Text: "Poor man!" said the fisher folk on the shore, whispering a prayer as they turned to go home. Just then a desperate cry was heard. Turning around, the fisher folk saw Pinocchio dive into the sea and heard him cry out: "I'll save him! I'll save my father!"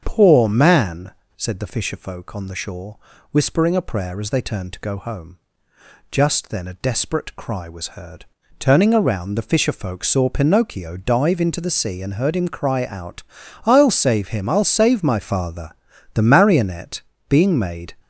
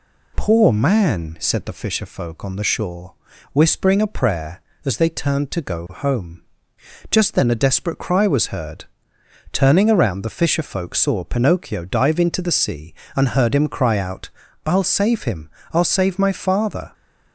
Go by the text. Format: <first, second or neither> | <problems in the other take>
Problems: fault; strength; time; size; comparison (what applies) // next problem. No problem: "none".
second | starts louder than the rest; until 1.0 s; 7 dB // goes on to say "The Marionette being made"; strong; from 16.1 s on; 1.8 s long